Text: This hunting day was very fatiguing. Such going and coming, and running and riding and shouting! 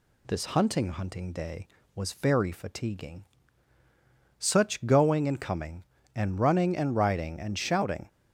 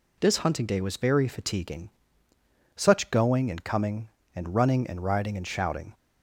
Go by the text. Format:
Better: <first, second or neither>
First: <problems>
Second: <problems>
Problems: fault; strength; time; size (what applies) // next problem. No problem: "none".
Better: second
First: says "hunting" twice; at 0.8 s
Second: none